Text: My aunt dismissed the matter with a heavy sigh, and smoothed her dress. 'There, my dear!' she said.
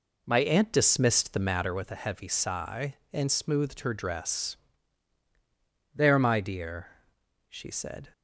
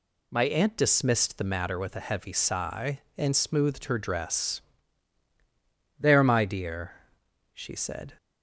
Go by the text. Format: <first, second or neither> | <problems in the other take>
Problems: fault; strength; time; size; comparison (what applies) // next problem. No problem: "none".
second | starts louder than the rest; until 1.9 s; 3.5 dB